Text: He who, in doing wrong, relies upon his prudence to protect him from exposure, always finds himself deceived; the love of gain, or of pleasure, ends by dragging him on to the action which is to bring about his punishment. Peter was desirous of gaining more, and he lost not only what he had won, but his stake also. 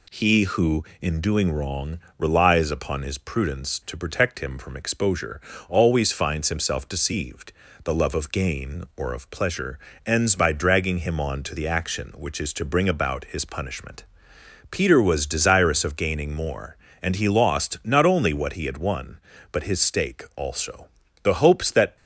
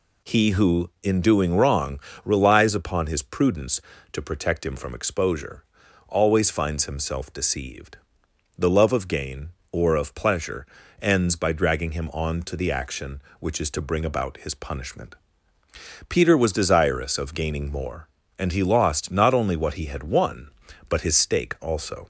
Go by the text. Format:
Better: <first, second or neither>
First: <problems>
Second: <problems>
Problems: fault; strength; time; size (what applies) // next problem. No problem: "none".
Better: second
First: goes on to say "The hopes that"; noticeable; from 21.2 s on; 0.74 s long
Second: none